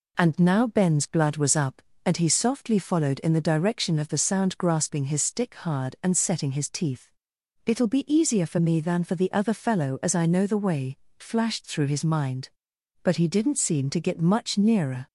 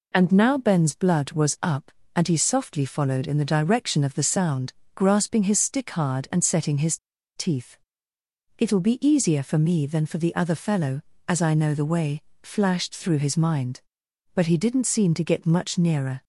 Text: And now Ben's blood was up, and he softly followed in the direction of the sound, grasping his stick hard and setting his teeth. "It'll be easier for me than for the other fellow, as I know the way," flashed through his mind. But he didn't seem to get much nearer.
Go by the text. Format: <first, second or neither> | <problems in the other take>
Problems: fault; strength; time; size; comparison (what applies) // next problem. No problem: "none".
first | pauses between "his" and "teeth"; at 6.9 s; 0.38 s long